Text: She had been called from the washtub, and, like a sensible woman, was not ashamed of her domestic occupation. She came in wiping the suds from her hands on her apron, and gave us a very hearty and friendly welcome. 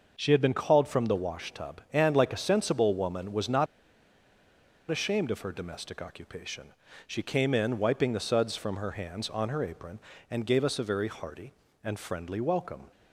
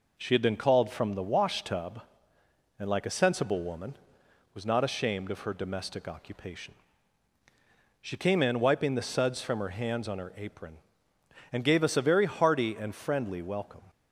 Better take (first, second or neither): second